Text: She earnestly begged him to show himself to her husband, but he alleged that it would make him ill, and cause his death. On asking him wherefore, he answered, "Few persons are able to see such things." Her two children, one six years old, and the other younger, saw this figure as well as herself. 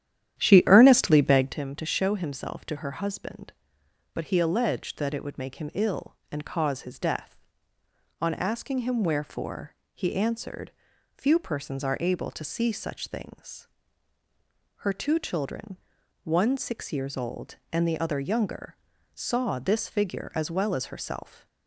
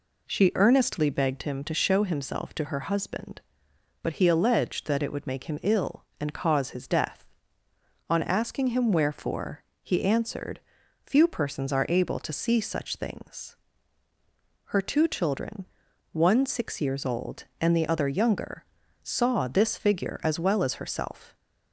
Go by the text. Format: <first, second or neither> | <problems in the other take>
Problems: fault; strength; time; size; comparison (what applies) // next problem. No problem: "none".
second | starts louder than the rest; strong; until 1.7 s; 10.5 dB